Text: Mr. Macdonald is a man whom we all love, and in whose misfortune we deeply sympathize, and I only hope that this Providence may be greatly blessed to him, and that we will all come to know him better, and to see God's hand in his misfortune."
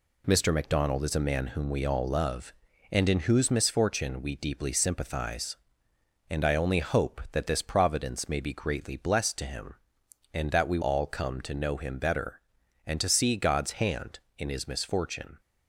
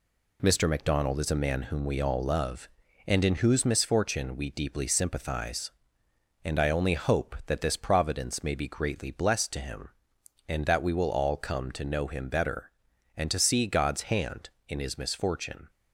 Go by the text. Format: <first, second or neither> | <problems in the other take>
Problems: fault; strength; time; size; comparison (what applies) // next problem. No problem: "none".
second | skips "will"; at 10.8 s